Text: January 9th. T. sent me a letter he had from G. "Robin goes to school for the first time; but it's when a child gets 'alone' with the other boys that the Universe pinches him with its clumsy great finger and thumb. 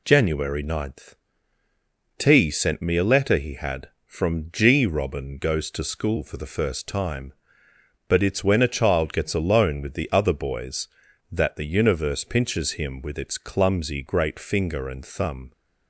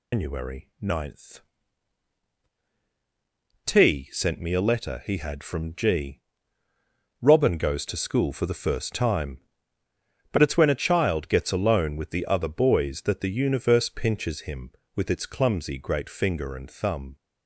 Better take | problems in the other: first | loses the start of "January"; at 0.1 s; 165 ms

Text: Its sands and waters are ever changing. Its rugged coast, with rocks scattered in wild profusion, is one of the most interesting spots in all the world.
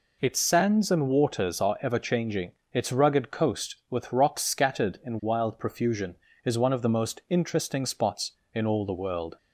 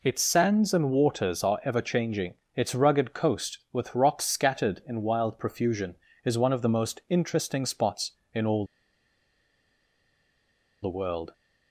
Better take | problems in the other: first | pauses between "all" and "the"; strong; at 8.6 s; 2.1 s long

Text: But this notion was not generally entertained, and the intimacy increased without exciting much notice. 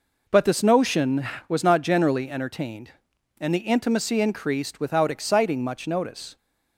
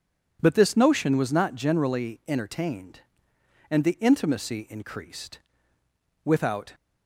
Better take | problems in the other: first | pauses between "increased" and "without"; noticeable; at 5.3 s; 0.86 s long // stops before "exciting much notice"; at 6.7 s

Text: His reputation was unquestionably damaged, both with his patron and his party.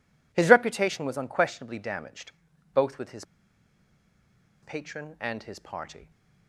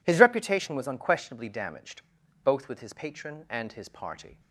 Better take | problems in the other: second | pauses between "his" and "patron"; strong; at 3.2 s; 1.3 s long

